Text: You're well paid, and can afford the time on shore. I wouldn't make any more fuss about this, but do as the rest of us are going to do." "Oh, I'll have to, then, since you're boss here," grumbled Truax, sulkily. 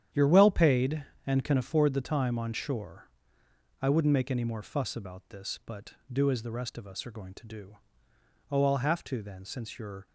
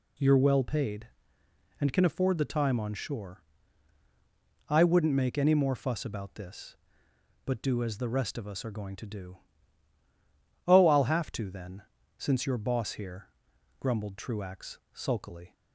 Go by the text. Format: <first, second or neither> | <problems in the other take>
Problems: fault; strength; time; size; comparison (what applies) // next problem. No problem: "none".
second | starts louder than the rest; strong; until 1.3 s; 9.5 dB // stops before "boss here grumbled Truax sulkily"; at 10.0 s